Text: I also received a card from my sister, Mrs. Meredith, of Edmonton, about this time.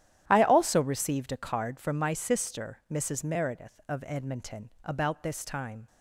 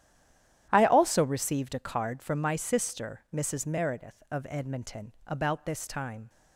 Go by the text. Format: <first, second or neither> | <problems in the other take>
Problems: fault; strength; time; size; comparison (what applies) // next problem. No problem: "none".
first | stays silent before the first word; slight; until 0.6 s; 0.6 s long // starts louder than the rest; strong; until 1.7 s; 11 dB; strong in the first